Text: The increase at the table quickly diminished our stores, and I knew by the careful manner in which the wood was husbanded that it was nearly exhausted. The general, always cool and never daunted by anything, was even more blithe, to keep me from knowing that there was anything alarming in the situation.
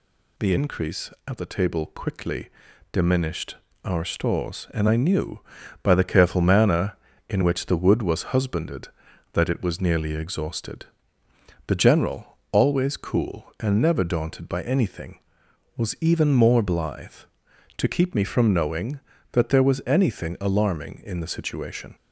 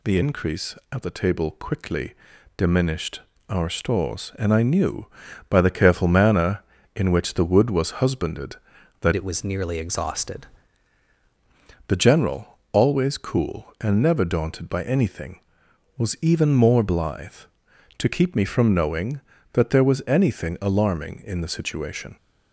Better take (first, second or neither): first